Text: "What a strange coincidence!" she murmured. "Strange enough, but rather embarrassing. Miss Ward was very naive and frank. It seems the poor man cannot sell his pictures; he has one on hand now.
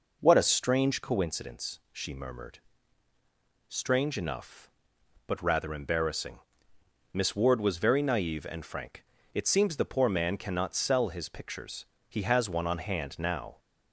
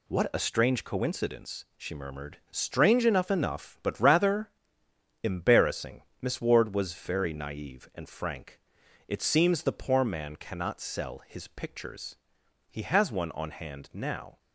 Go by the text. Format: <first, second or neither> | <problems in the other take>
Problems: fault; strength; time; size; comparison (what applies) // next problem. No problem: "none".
first | says "enough" twice; at 3.2 s // pauses between "rather" and "embarrassing"; noticeable; at 4.5 s; 0.72 s long